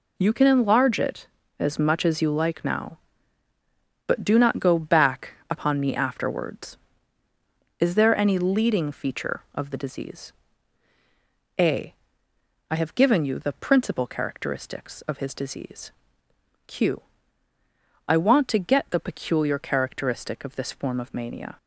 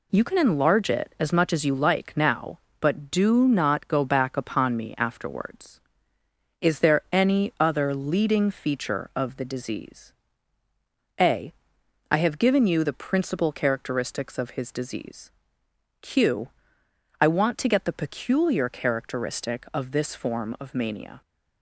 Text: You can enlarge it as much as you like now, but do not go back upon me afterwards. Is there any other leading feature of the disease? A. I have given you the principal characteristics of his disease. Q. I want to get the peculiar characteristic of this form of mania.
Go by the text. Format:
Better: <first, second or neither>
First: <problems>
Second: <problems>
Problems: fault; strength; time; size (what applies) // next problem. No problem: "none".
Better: second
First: pauses between "back" and "upon"; slight; at 5.3 s; 0.16 s long // skips "other"; at 8.3 s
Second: none